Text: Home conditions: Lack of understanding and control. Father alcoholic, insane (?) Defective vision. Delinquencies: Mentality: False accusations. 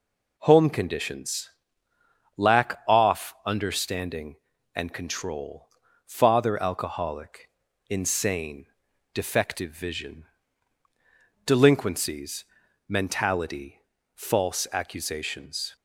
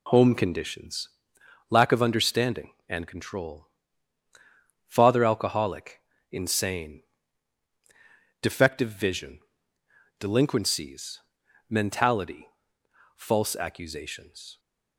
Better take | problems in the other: second | says "off" for "of"; at 2.8 s

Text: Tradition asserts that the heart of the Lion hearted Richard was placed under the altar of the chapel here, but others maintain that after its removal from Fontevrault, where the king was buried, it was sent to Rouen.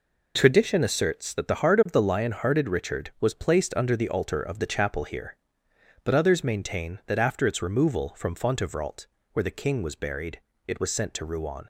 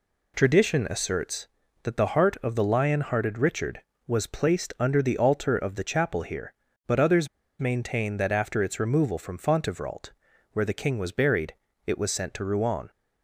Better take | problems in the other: first | pauses between "others" and "maintain"; slight; at 7.2 s; 0.31 s long

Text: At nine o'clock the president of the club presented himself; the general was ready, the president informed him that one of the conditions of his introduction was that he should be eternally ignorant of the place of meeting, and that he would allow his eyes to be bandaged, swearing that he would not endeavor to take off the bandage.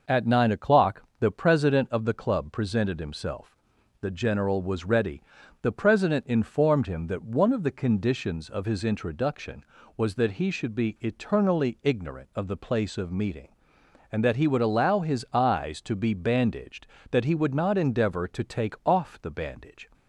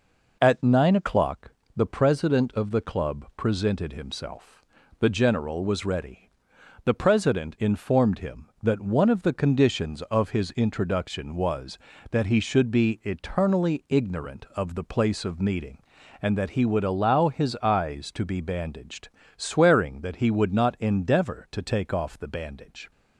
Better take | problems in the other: second | pauses between "o'clock" and "the"; slight; at 1.0 s; 0.16 s long; slight in the second // skips "swearing"; at 16.9 s

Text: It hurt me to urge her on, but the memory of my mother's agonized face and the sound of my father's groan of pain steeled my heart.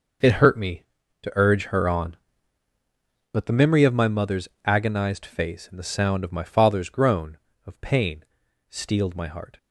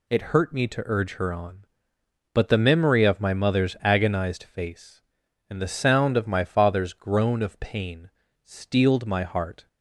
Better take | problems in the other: second | gets quieter; strong; throughout; 12.5 dB // pauses between "mother's" and "agonized"; slight; at 4.4 s; 0.16 s long // pauses between "pain" and "steeled"; noticeable; at 8.2 s; 0.46 s long; slight in the second

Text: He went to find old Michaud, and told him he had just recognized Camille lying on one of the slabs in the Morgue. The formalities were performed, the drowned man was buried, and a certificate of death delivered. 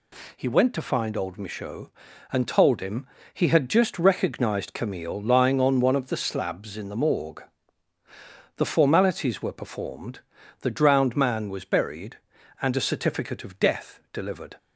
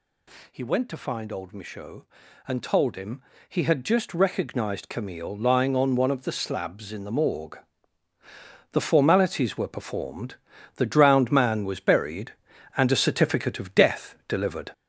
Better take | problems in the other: first | gets louder; noticeable; throughout; 5 dB // pauses between "him" and "he"; slight; at 3.2 s; 0.26 s long; slight in the first

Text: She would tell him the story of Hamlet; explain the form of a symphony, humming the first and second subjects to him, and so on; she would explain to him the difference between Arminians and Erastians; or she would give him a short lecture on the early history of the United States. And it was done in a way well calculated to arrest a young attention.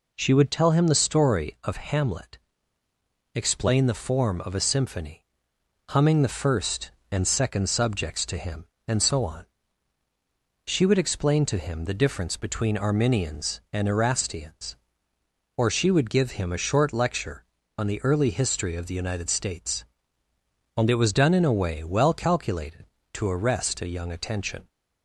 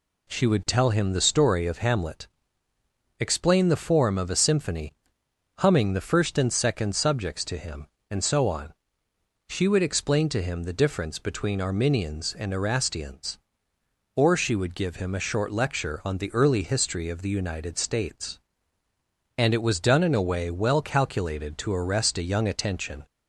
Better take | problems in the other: neither | none

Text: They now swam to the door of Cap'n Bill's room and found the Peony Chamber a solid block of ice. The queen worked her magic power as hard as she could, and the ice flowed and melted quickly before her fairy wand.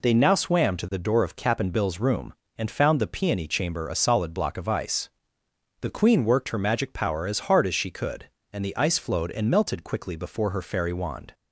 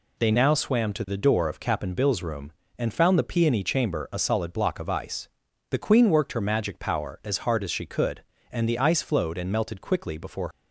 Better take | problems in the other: first | stops before "her fairy wand"; at 10.5 s

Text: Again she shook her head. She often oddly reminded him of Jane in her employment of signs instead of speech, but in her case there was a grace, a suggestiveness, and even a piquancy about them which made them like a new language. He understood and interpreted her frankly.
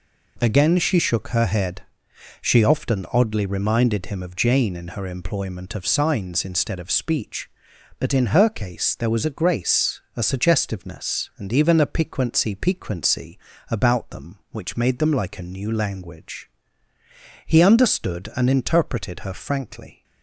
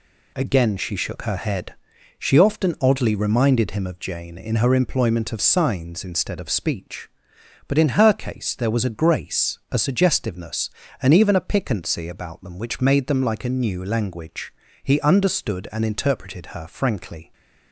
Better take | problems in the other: second | says "piquancy" twice; at 12.5 s

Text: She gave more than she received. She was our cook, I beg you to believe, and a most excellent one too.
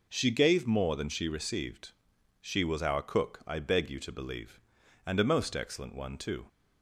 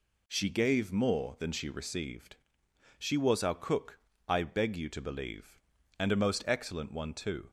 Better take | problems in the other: neither | none

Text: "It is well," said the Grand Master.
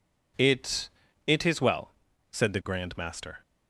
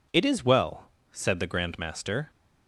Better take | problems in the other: second | says "It" twice; at 1.2 s

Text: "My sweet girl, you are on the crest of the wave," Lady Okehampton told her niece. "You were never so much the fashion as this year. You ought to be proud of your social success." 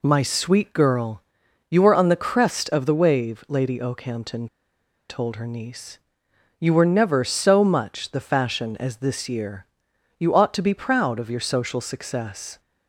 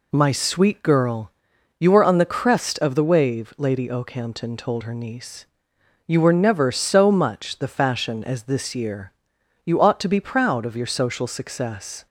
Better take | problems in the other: second | pauses between "Okehampton" and "told"; noticeable; at 4.4 s; 0.62 s long

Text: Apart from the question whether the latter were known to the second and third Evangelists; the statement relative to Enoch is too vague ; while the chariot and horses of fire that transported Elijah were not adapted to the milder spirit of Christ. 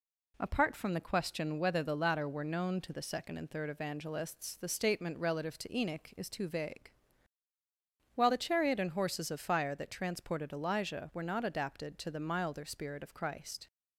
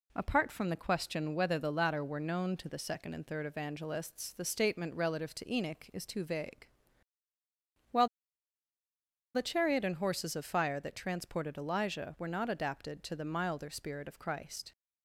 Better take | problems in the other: first | pauses between "while" and "the"; strong; at 8.0 s; 1.2 s long

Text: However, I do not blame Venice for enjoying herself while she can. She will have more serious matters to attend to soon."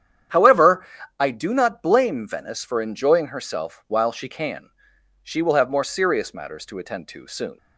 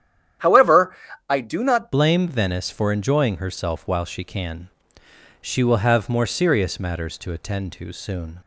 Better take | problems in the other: first | starts louder than the rest; strong; until 1.7 s; 10.5 dB; strong in the first // changes voice at "blame"; from 1.9 s on; 6.4 s long

